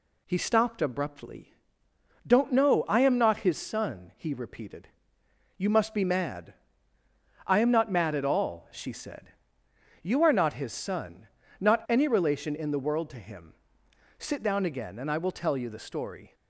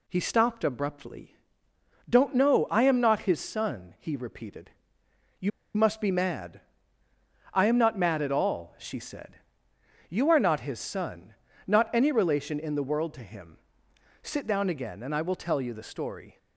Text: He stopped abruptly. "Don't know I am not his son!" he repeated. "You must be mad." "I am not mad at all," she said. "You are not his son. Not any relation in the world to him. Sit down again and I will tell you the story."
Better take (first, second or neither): first